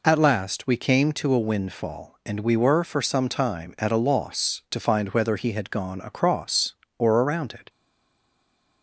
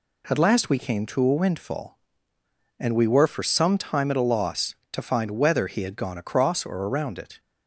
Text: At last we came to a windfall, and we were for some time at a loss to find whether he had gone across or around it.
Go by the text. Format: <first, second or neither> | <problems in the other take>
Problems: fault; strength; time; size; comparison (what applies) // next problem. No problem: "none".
second | stays silent after the last word; from 7.6 s on; 1.2 s long